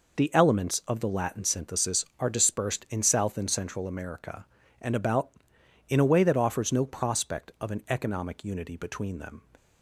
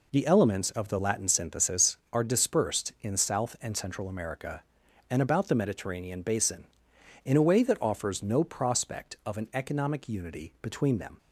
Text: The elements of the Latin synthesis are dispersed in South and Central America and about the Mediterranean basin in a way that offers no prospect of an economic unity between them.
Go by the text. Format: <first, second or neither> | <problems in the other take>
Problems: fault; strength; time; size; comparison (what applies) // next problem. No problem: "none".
second | skips "the Mediterranean basin"; at 5.5 s